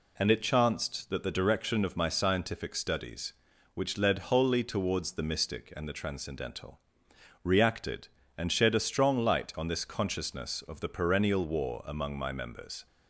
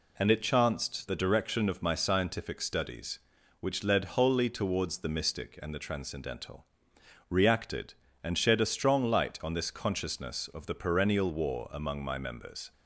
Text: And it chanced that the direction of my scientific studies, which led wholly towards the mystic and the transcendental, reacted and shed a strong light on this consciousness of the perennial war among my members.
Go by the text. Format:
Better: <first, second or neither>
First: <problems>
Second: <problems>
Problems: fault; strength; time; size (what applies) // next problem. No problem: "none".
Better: first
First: none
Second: skips "that"; at 1.0 s